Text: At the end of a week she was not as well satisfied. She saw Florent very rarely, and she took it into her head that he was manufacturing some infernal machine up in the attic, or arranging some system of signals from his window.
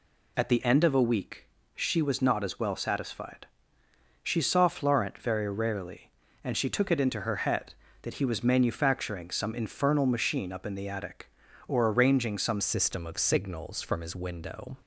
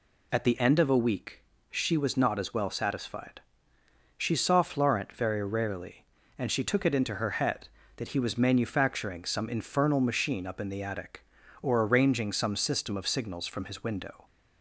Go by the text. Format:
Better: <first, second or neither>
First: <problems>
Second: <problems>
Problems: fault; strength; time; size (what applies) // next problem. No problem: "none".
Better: second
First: pauses between "week" and "she"; slight; at 1.4 s; 0.28 s long // changes voice at "system"; from 12.6 s on; 2.1 s long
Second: pauses between "week" and "she"; slight; at 1.4 s; 0.28 s long